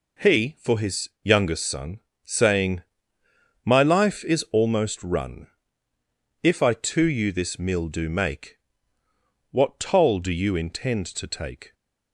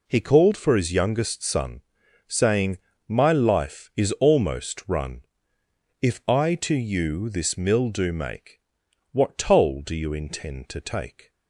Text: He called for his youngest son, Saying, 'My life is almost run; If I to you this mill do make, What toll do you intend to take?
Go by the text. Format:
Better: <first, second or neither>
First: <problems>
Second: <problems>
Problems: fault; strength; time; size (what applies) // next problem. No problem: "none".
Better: second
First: skips "called"; at 0.5 s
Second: none